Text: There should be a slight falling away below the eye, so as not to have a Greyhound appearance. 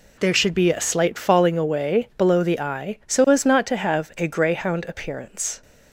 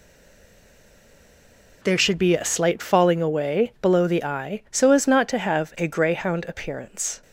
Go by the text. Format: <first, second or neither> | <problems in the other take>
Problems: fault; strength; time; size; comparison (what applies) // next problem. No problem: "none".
first | stays silent before the first word; noticeable; until 1.8 s; 1.8 s long